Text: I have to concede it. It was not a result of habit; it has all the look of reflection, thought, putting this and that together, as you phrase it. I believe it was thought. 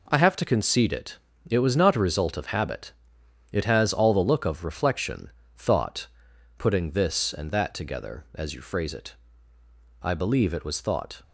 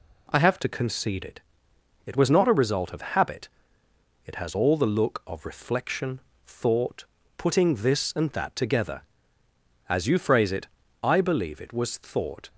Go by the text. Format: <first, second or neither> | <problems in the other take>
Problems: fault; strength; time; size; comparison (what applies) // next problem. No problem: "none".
first | changes voice at "to"; from 0.5 s on; 11.9 s long